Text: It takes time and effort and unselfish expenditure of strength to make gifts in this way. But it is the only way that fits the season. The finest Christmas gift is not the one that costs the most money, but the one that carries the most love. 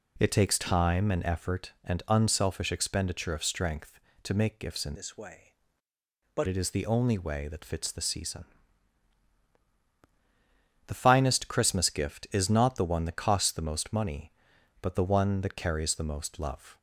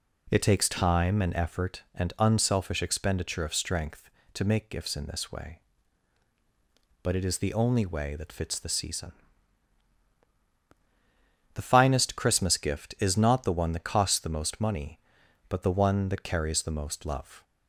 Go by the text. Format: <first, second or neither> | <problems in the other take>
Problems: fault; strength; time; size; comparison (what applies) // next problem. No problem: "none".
second | changes voice from "this" to "But"; from 4.9 to 6.4 s; 1.5 s long